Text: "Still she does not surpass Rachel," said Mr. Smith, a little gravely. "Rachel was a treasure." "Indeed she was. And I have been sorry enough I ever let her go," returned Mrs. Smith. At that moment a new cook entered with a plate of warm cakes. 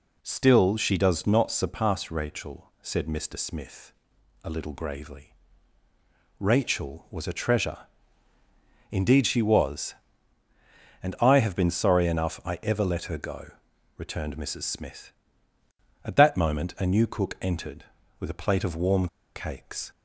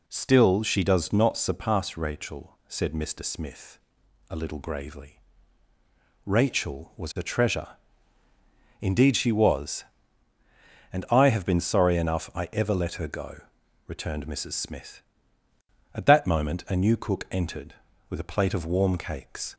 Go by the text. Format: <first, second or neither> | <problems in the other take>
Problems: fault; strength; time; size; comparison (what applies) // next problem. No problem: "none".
second | pauses between "warm" and "cakes"; slight; at 19.0 s; 0.27 s long